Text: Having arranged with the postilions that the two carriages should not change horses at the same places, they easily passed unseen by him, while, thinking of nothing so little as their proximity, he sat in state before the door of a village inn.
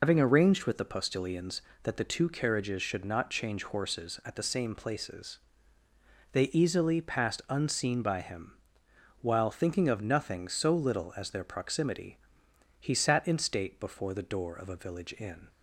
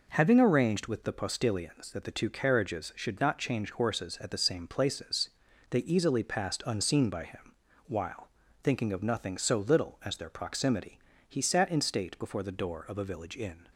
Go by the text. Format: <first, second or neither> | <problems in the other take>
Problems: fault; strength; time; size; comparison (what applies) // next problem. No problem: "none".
second | loses the start of "Having"; at 0.0 s; 90 ms